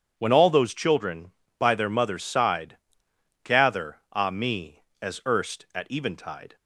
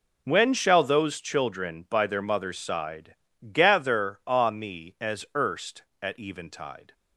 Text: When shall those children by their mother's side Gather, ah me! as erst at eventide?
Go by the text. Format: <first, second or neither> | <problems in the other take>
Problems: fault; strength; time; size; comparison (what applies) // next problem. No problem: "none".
second | says "all" for "shall"; at 0.3 s // pauses between "side" and "Gather"; noticeable; at 2.7 s; 0.66 s long; slight in the second